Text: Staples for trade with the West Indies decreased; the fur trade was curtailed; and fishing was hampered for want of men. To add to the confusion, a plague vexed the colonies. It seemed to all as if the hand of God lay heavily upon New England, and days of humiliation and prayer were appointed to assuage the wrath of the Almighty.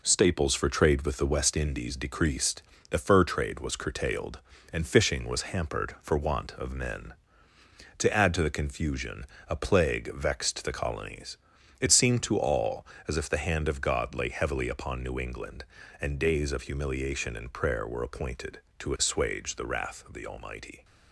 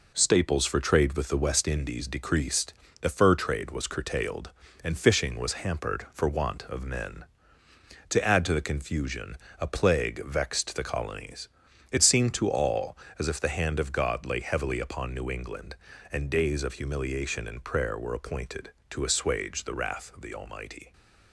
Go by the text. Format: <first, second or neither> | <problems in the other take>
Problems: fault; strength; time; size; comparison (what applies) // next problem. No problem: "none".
neither | none